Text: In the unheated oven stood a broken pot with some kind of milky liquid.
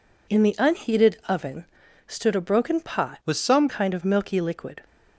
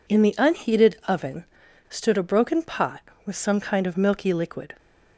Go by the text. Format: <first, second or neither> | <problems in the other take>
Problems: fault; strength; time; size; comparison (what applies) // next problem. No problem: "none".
second | pauses between "oven" and "stood"; at 1.6 s; 0.42 s long; also in the second // changes voice from "with" to "some"; from 3.2 to 3.6 s; 0.4 s long